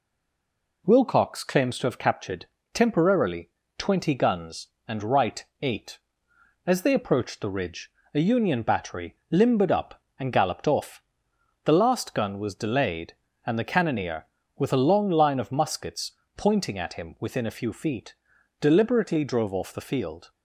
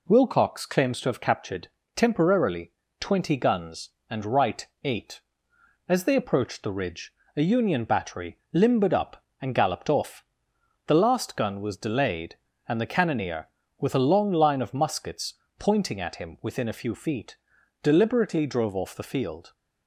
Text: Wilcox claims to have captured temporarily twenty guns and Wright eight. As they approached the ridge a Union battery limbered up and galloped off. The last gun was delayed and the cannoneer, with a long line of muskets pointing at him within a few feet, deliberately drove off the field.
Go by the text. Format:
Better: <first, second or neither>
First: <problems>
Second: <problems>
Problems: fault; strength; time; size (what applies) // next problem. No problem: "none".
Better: second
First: stays silent before the first word; slight; until 0.8 s; 0.8 s long // pauses between "captured" and "temporarily"; slight; at 2.4 s; 0.28 s long // pauses between "temporarily" and "twenty"; slight; at 3.4 s; 0.28 s long // pauses between "Wright" and "eight"; slight; at 5.4 s; 0.16 s long // pauses between "ridge" and "a"; slight; at 7.8 s; 0.24 s long // pauses between "battery" and "limbered"; slight; at 9.1 s; 0.16 s long // pauses between "muskets" and "pointing"; slight; at 16.1 s; 0.24 s long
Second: pauses between "captured" and "temporarily"; slight; at 1.6 s; 0.28 s long // pauses between "temporarily" and "twenty"; slight; at 2.7 s; 0.28 s long // pauses between "Wright" and "eight"; slight; at 4.6 s; 0.16 s long // pauses between "ridge" and "a"; slight; at 7.1 s; 0.24 s long // pauses between "battery" and "limbered"; slight; at 8.3 s; 0.16 s long // pauses between "muskets" and "pointing"; slight; at 15.3 s; 0.24 s long